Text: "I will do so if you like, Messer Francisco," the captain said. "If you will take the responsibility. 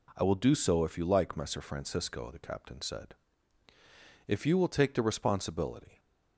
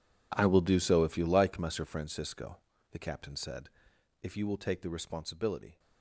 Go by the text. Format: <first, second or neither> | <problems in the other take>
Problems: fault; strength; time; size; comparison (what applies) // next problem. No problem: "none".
first | gets quieter; strong; throughout; 17 dB